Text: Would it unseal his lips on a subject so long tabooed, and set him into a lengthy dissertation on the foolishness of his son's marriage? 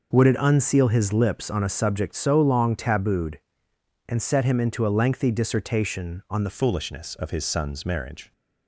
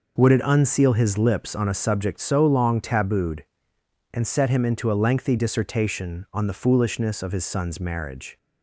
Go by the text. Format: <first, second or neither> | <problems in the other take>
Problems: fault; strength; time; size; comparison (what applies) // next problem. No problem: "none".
second | changes voice at "foolishness"; from 6.4 s on; 1.9 s long